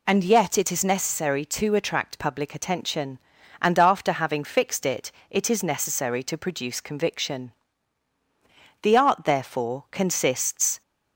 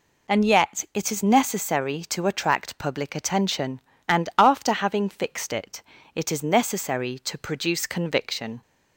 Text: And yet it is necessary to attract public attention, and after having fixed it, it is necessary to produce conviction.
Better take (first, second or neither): second